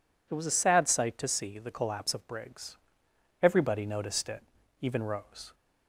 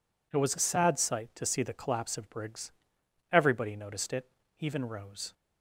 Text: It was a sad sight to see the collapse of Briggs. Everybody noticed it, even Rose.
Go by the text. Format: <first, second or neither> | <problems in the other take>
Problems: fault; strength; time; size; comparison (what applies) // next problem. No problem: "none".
neither | none